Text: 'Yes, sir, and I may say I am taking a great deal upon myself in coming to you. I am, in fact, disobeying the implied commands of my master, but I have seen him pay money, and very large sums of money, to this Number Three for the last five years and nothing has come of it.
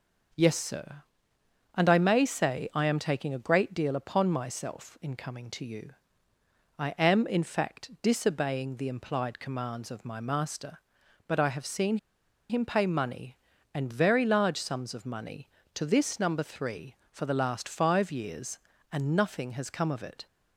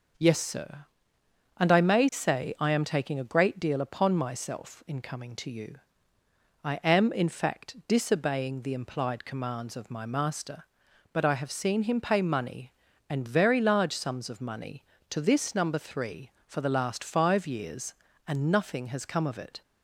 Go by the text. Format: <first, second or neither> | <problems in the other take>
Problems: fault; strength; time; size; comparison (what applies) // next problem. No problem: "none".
second | pauses between "seen" and "him"; noticeable; at 11.9 s; 0.52 s long